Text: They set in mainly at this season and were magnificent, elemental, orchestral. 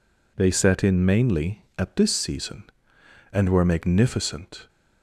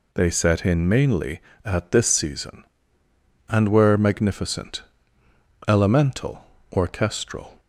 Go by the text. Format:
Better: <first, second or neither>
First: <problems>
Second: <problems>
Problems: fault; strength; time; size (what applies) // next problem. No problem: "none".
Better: second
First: stops before "elemental orchestral"; at 4.6 s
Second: none